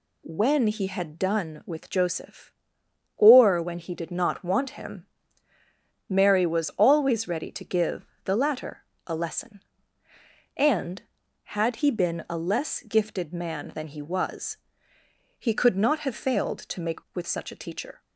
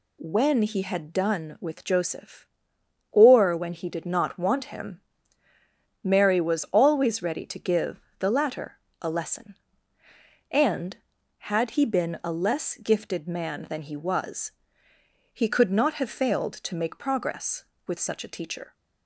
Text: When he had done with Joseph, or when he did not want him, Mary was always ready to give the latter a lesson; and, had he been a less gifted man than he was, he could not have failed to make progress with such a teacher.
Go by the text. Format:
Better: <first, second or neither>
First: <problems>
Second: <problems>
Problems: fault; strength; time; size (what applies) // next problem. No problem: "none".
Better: second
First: pauses between "give" and "the"; slight; at 8.0 s; 0.18 s long // pauses between "latter" and "a"; slight; at 8.8 s; 0.22 s long // skips "progress"; at 17.0 s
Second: pauses between "give" and "the"; slight; at 8.0 s; 0.18 s long // pauses between "latter" and "a"; slight; at 8.7 s; 0.22 s long